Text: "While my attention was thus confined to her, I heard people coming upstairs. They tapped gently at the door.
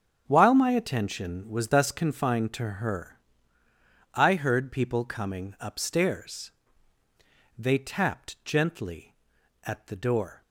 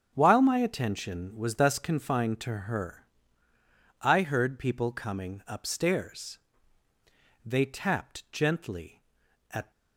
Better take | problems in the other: first | starts louder than the rest; strong; until 1.1 s; 7.5 dB; strong in the first // stops before "the door"; at 9.7 s

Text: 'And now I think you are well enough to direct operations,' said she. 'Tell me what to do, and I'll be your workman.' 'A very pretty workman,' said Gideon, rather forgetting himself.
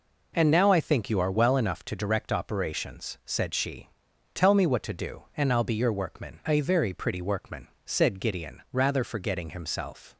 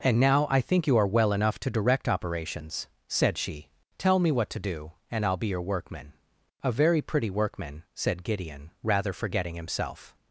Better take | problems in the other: neither | none

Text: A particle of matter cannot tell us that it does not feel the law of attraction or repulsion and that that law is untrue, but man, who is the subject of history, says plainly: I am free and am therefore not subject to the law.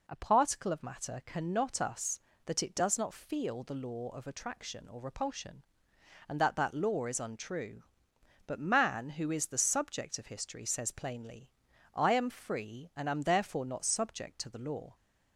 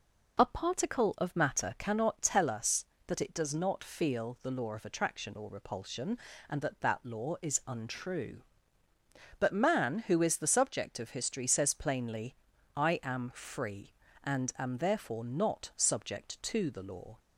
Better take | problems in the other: second | skips "tell"; at 1.8 s

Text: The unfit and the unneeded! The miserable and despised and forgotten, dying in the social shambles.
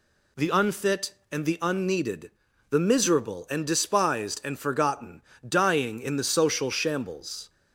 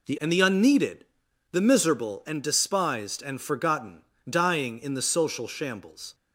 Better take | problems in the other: first | skips "unfit"; at 0.1 s

